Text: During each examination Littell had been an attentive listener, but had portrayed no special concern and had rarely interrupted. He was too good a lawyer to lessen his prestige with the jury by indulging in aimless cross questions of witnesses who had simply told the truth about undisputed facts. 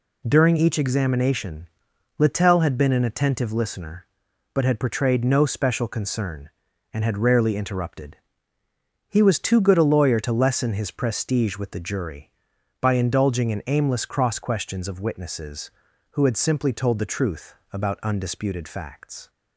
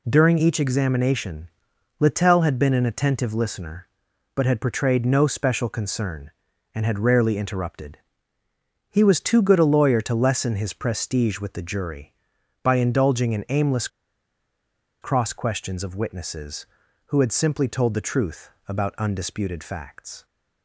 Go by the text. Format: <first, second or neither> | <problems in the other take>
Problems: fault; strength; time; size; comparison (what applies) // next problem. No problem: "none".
first | pauses between "examination" and "Littell"; noticeable; at 1.4 s; 0.50 s long; noticeable in the first // pauses between "aimless" and "cross"; at 13.8 s; 1.1 s long // pauses between "truth" and "about"; slight; at 18.4 s; 0.18 s long; slight in the first